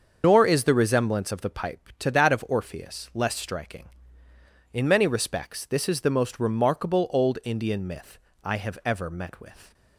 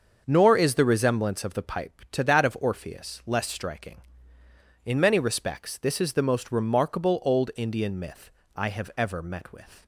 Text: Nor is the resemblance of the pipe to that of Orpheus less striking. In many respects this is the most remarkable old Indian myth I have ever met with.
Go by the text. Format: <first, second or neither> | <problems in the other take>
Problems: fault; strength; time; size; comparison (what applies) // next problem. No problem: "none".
second | loses the start of "Nor"; at 0.2 s; 85 ms // starts louder than the rest; until 1.2 s; 7 dB; also in the second // pauses between "myth" and "I"; slight; at 8.1 s; 0.26 s long; slight in the second